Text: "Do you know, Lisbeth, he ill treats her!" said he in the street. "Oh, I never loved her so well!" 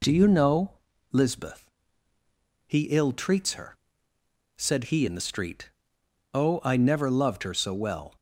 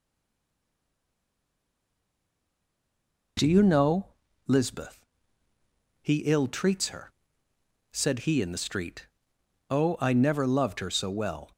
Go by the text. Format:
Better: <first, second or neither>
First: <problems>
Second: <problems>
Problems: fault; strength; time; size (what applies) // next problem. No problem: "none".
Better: first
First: none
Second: stays silent before the first word; strong; until 3.3 s; 3.3 s long